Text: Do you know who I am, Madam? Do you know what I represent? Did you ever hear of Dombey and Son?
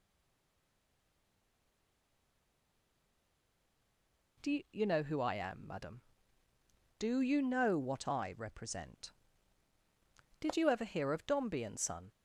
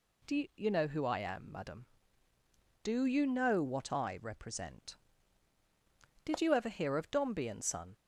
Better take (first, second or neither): second